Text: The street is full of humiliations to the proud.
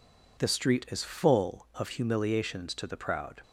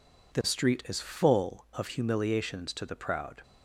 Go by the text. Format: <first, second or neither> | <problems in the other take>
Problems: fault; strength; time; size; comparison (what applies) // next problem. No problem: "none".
neither | none